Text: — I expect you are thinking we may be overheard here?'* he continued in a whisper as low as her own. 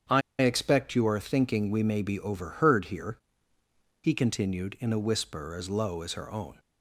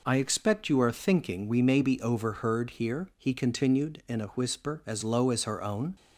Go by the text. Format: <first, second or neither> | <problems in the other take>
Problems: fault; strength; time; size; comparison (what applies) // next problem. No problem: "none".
second | starts louder than the rest; strong; until 1.3 s; 8 dB // pauses between "I" and "expect"; slight; at 0.2 s; 0.20 s long